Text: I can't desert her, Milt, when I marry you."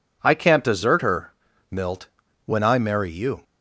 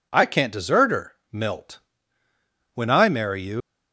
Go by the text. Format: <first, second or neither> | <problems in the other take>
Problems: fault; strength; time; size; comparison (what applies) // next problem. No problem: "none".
first | leaves "you" unfinished; at 3.6 s; 105 ms